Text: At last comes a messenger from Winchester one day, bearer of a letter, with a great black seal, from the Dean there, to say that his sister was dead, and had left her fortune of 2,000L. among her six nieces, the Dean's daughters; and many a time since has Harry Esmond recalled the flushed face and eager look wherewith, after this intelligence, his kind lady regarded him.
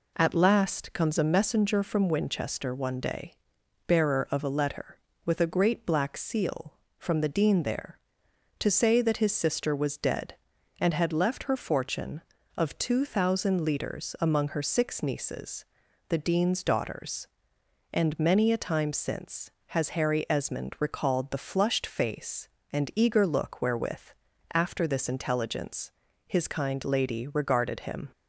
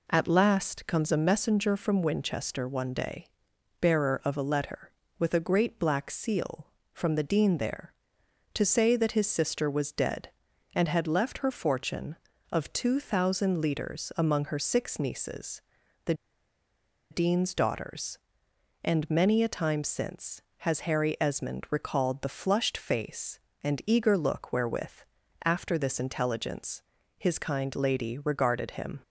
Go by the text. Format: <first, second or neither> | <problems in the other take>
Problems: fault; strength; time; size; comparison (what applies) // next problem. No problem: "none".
first | pauses between "the" and "Dean's"; noticeable; at 16.1 s; 0.97 s long